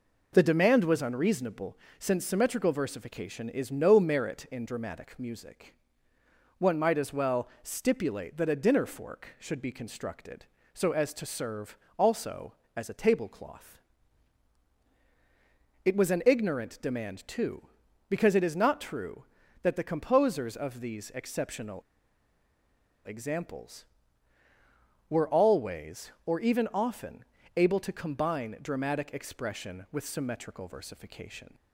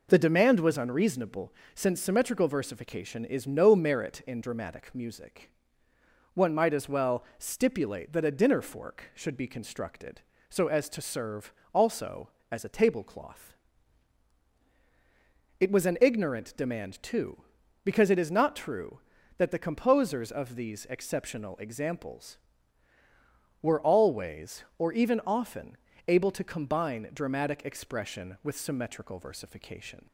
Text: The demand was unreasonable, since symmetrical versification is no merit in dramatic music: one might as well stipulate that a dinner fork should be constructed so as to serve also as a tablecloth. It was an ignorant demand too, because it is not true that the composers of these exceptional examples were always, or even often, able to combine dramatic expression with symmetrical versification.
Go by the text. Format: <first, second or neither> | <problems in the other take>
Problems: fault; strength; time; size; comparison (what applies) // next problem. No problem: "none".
second | pauses between "serve" and "also"; slight; at 11.7 s; 0.18 s long; slight in the second // pauses between "exceptional" and "examples"; strong; at 21.7 s; 1.2 s long